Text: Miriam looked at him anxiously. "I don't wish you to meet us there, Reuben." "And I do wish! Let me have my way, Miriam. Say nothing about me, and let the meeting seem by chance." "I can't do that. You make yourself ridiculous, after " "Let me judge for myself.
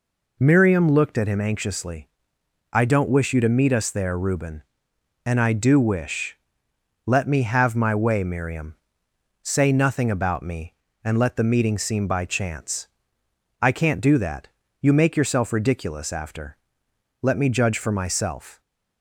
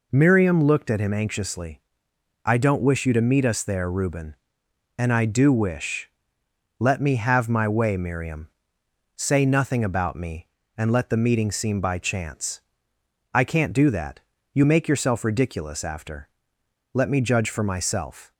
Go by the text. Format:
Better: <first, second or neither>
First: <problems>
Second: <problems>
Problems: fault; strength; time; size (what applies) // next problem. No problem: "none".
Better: neither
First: none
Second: none